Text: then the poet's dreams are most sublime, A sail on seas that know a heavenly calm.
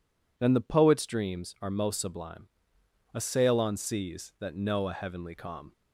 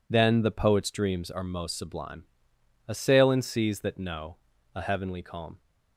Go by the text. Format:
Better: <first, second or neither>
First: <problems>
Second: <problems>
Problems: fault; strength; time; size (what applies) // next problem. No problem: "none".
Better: first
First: none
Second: says "in" for "on"; at 3.2 s // pauses between "know" and "a"; slight; at 4.3 s; 0.36 s long